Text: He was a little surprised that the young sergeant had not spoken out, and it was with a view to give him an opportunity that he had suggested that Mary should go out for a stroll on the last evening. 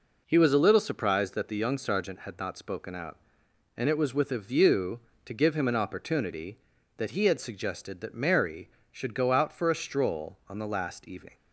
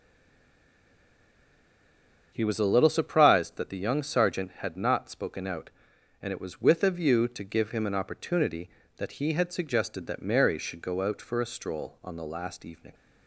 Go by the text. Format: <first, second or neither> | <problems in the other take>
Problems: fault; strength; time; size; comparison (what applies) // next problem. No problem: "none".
first | stays silent before the first word; until 2.3 s; 2.3 s long // starts louder than the rest; strong; until 3.3 s; 7.5 dB